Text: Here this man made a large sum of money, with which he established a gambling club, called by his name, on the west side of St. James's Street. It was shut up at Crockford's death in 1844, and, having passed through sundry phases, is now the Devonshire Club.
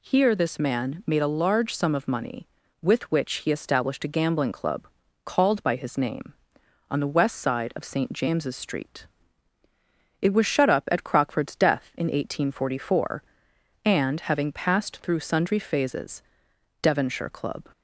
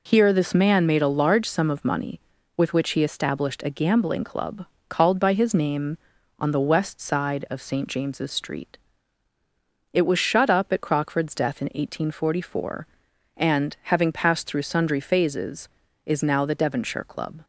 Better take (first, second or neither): second